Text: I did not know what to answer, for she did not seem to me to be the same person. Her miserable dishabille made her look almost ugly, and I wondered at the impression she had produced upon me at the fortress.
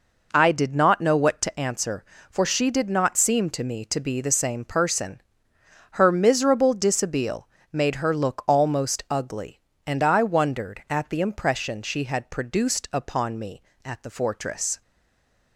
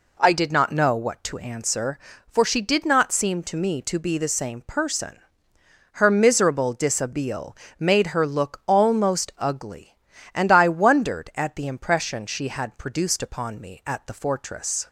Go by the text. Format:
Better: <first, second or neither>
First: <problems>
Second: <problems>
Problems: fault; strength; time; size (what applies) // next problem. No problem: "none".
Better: second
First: pauses between "dishabille" and "made"; slight; at 7.4 s; 0.26 s long // stays silent after the last word; slight; from 14.8 s on; 0.7 s long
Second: pauses between "dishabille" and "made"; slight; at 7.5 s; 0.22 s long